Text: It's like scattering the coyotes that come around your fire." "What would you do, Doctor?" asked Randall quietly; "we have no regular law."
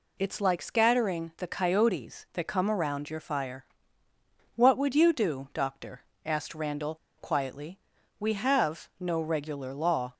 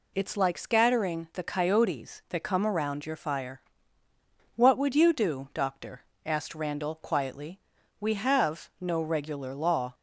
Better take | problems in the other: second | pauses between "Randall" and "quietly"; slight; at 6.9 s; 0.22 s long

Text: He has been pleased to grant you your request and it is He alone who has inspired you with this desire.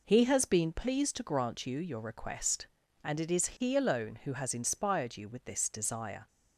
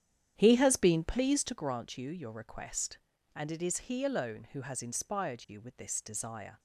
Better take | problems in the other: first | starts louder than the rest; strong; until 1.6 s; 10 dB

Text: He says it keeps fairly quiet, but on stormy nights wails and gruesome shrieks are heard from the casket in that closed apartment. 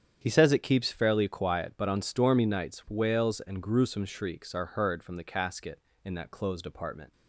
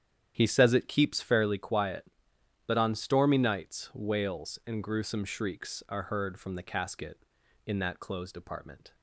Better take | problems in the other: neither | starts louder than the rest; strong; the same in both

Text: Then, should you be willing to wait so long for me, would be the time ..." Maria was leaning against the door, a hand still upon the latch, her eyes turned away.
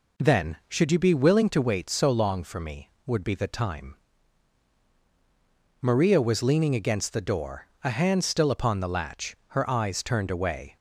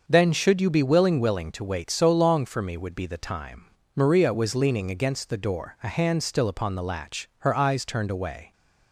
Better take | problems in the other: first | starts louder than the rest; until 1.0 s; 6.5 dB // says "willing" twice; at 1.2 s

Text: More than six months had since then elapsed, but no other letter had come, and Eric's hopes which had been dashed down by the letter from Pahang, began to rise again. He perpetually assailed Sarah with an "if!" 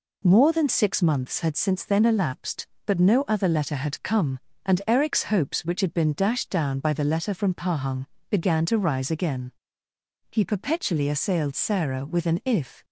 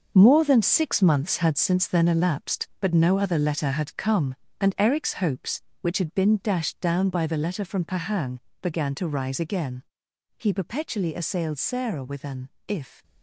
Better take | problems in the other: first | gets quieter; strong; throughout; 9 dB // pauses between "an" and "if"; slight; at 12.4 s; 0.18 s long

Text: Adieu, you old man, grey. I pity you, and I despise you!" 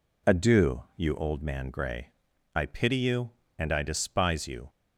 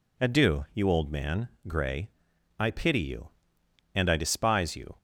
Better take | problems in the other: neither | none

